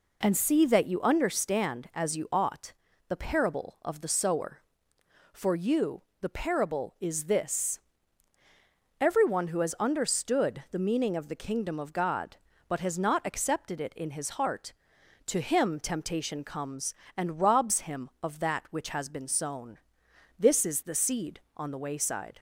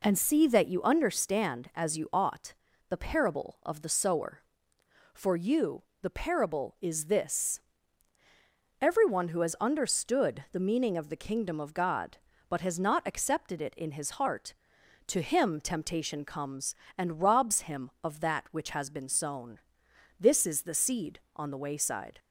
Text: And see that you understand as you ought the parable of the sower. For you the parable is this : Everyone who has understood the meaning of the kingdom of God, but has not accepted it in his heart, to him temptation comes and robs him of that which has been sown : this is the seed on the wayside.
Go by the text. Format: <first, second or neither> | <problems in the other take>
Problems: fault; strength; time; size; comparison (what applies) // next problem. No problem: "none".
neither | pauses between "ought" and "the"; slight; the same in both // pauses between "you" and "the"; slight; the same in both